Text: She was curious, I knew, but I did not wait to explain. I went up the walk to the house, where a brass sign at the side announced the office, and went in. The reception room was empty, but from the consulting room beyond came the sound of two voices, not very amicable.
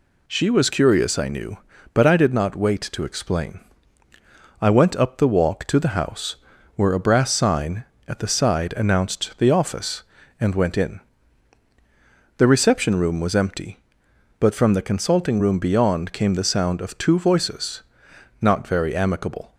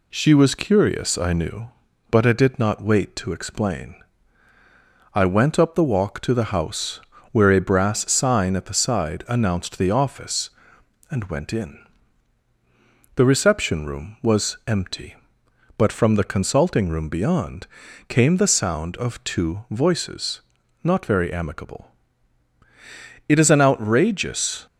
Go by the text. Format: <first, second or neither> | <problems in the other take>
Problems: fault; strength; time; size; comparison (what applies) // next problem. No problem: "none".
first | pauses between "beyond" and "came"; at 17.6 s; 0.40 s long // goes on to say "It is an outrageous"; from 23.2 s on; 1.3 s long